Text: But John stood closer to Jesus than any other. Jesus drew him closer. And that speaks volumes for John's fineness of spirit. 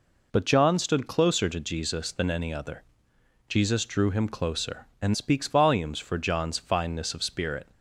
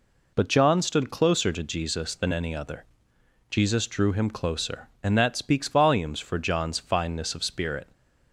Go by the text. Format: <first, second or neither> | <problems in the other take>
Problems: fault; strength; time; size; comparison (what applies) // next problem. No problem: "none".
second | skips "that"; at 5.1 s